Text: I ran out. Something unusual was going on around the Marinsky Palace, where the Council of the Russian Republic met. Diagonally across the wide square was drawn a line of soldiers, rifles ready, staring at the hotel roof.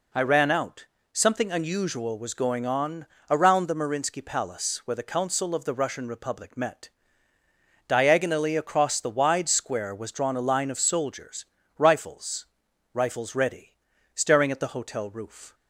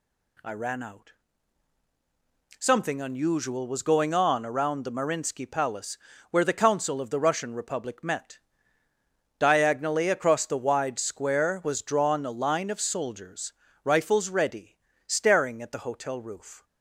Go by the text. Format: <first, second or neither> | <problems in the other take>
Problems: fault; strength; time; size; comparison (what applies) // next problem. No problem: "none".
second | pauses between "on" and "around"; slight; at 3.0 s; 0.24 s long // says "rifles" twice; at 12.9 s